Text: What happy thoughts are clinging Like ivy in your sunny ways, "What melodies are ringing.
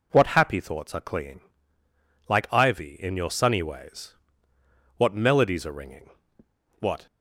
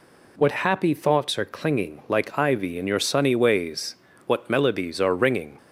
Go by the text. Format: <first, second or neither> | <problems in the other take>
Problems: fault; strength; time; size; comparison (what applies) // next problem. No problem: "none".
second | pauses between "clinging" and "Like"; noticeable; at 1.3 s; 0.88 s long // goes on to say "What"; slight; from 6.7 s on; 0.26 s long